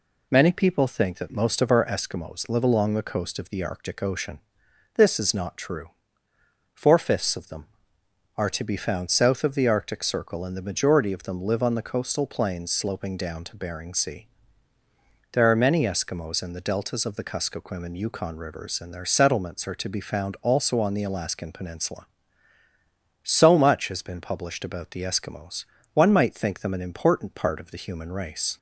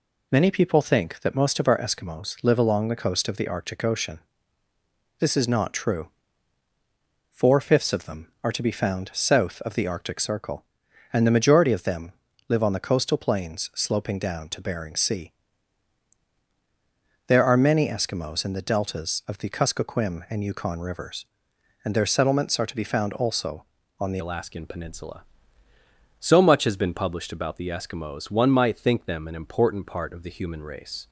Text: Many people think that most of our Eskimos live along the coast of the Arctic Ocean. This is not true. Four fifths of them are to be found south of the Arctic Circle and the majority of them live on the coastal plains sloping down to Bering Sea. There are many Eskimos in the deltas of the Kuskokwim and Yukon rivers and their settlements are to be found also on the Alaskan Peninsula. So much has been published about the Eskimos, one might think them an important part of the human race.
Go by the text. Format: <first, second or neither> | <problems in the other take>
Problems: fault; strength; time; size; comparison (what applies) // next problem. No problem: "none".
first | pauses between "them" and "live"; at 12.1 s; 0.38 s long // changes voice at "Alaskan"; from 24.1 s on; 6.9 s long